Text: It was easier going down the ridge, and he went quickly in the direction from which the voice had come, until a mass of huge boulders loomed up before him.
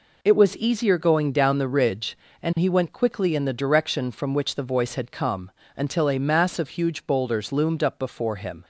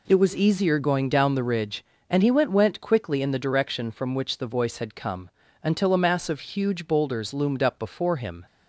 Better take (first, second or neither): first